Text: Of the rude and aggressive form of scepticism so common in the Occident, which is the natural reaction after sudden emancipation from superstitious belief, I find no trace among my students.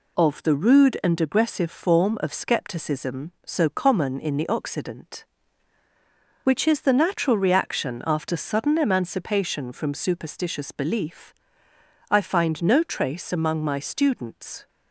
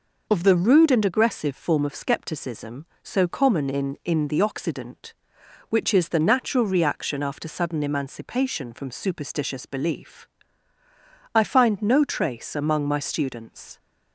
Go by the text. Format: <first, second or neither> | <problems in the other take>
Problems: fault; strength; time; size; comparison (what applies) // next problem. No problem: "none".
first | says "in" twice; at 4.0 s